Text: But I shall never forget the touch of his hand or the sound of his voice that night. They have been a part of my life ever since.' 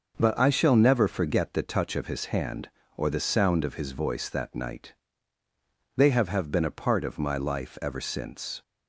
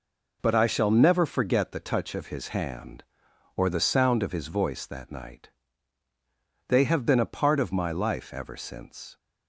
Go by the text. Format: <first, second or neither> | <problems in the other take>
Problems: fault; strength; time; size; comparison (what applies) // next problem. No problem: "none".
second | says "have" twice; at 6.2 s